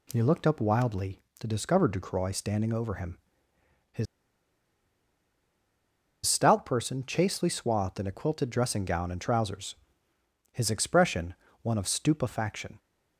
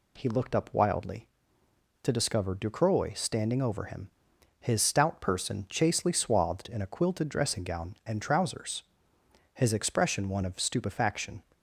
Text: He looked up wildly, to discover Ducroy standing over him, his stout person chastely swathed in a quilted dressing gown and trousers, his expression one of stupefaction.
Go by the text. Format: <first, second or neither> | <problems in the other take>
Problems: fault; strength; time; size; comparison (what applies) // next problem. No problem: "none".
second | pauses between "his" and "stout"; strong; at 4.0 s; 2.2 s long // pauses between "expression" and "one"; slight; at 11.3 s; 0.28 s long